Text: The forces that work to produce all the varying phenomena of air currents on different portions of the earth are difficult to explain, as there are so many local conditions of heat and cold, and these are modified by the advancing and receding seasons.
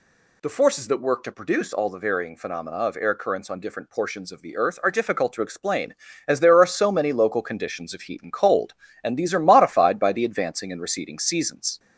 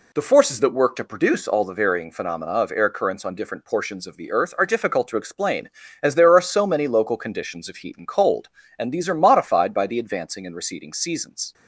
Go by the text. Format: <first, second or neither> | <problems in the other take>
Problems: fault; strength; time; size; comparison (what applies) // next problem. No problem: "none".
second | gets louder; slight; throughout; 2 dB